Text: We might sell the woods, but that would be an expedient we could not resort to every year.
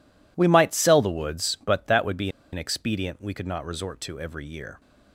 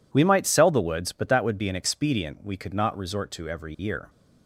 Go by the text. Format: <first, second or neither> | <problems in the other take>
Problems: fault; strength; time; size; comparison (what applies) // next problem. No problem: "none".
second | pauses between "be" and "an"; slight; at 2.2 s; 0.24 s long